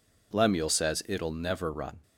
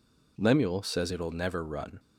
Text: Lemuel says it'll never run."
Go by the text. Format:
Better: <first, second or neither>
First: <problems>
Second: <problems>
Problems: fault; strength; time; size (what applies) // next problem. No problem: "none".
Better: neither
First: none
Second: none